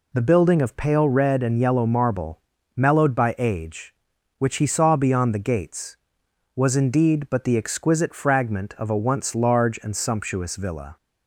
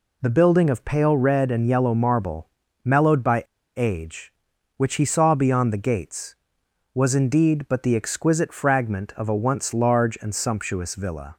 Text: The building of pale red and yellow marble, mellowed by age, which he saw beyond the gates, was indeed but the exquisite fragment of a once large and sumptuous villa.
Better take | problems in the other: first | pauses between "by" and "age"; slight; at 3.4 s; 0.33 s long

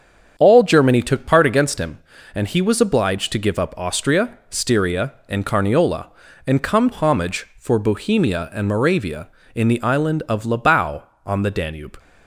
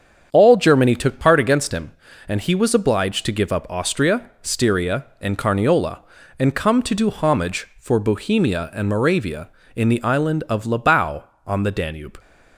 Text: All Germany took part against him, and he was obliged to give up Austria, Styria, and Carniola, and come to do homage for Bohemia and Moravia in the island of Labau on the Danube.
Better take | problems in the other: second | starts louder than the rest; strong; until 1.3 s; 7.5 dB; strong in the second // skips "to do"; at 6.9 s

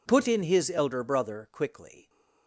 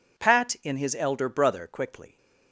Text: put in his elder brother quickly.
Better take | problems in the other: first | says "pat" for "put"; at 0.1 s

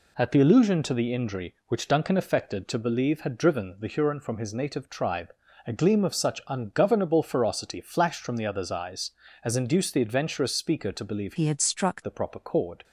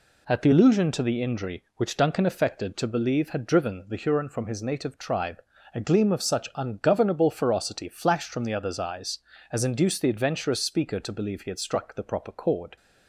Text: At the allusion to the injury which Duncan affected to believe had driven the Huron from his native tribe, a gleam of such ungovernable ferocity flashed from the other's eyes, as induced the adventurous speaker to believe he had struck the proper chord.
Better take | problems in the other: second | changes voice from "he" to "struck"; from 11.3 to 12.0 s; 0.7 s long

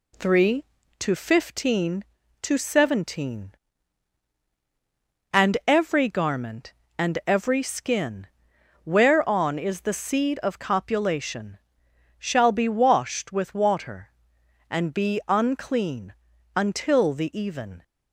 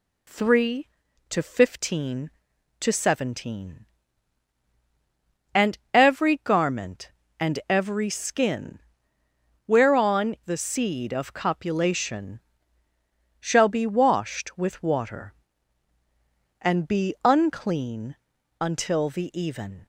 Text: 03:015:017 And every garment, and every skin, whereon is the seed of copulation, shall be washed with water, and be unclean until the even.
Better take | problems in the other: first | skips "is"; at 10.3 s // pauses between "unclean" and "until"; at 18.1 s; 0.44 s long; also in the first

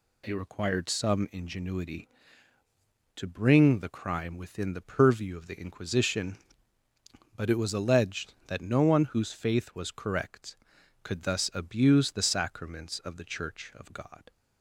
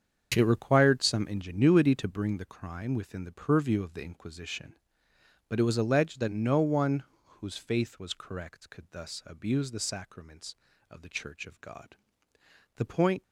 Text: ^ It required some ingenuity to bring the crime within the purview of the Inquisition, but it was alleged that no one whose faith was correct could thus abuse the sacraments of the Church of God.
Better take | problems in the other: first | starts louder than the rest; strong; until 1.3 s; 7.5 dB // pauses between "one" and "whose"; slight; at 7.0 s; 0.22 s long // goes on to say "The point"; slight; from 12.7 s on; 0.46 s long

